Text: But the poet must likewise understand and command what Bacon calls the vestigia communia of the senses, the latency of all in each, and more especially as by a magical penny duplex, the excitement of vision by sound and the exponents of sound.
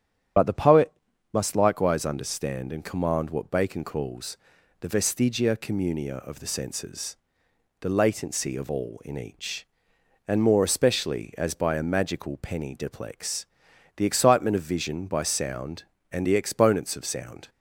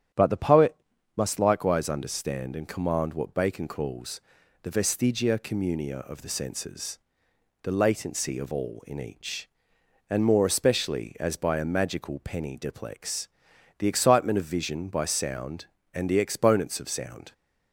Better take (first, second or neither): second